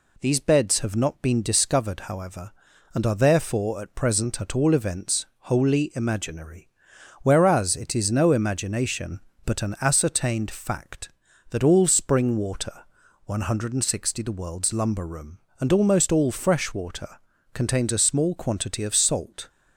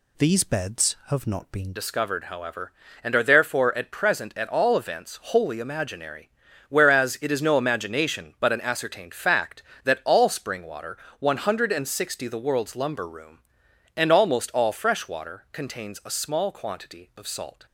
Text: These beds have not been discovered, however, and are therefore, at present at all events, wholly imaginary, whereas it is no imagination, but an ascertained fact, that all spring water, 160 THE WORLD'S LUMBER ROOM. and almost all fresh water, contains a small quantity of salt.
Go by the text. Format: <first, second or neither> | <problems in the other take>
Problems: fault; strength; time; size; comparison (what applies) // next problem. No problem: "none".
first | changes voice at "discovered"; from 1.7 s on; 15.9 s long